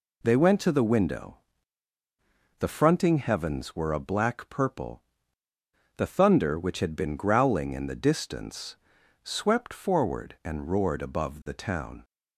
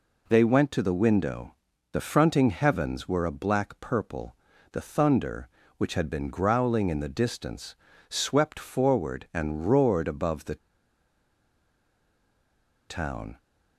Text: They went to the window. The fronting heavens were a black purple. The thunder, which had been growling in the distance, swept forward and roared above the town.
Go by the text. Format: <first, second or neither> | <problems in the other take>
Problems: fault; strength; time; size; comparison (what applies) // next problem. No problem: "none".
first | pauses between "the" and "town"; strong; at 10.5 s; 2.3 s long